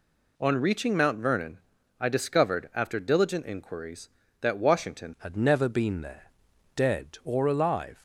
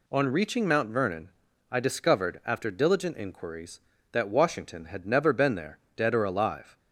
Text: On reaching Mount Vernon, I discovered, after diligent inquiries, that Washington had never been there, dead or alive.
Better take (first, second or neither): second